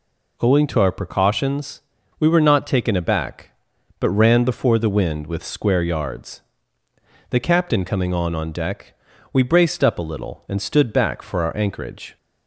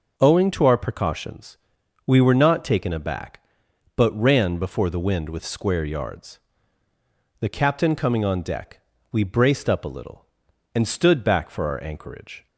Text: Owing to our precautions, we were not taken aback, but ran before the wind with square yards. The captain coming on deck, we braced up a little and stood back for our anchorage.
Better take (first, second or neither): second